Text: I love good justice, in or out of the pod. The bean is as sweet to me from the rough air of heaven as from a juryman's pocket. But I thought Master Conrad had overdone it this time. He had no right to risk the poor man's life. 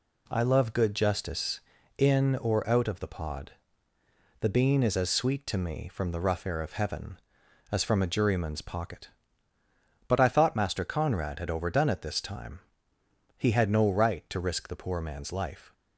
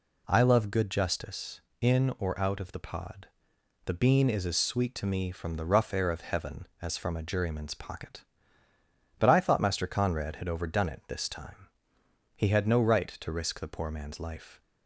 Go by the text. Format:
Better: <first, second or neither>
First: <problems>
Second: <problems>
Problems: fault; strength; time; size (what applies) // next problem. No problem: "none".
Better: neither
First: none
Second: none